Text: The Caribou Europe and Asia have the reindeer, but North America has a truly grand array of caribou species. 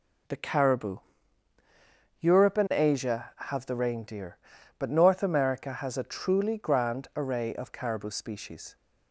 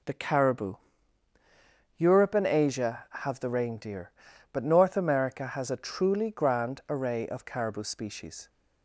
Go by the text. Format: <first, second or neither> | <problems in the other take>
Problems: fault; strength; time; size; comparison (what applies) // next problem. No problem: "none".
neither | pauses between "Caribou" and "Europe"; the same in both